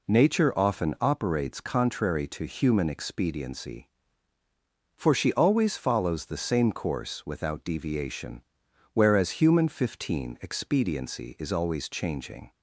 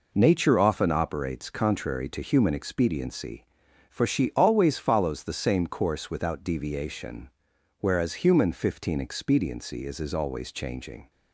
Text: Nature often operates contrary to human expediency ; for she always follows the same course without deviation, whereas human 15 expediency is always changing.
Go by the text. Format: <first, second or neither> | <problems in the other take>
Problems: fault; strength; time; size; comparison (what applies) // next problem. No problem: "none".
first | says "is" twice; at 9.9 s